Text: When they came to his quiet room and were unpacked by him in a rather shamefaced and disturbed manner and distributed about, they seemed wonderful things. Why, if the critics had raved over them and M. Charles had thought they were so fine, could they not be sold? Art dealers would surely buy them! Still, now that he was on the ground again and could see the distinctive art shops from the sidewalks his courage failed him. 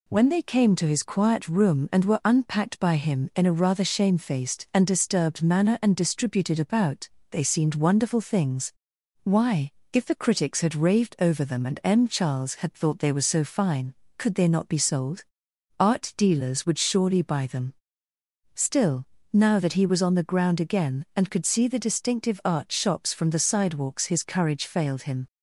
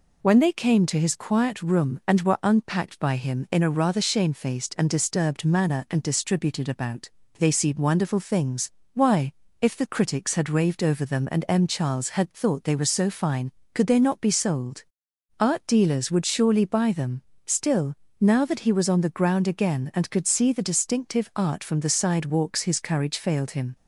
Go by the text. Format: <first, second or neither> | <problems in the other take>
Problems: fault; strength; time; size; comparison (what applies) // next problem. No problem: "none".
first | skips "shops"; at 21.6 s